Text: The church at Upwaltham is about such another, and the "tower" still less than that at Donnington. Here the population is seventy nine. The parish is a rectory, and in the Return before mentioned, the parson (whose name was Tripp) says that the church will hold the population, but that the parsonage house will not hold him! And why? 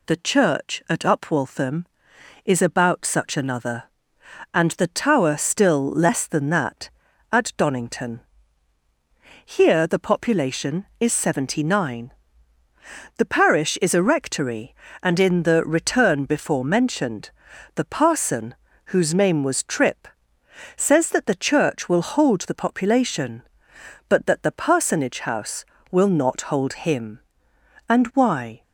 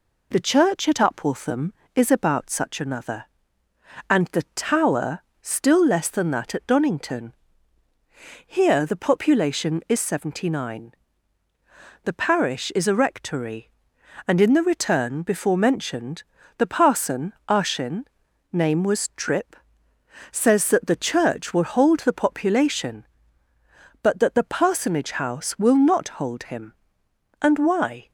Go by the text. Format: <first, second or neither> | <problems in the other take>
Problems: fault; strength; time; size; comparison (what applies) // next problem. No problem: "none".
first | pauses between "tower" and "still"; slight; at 5.1 s; 0.22 s long // says "arshin" for "whose"; at 17.4 s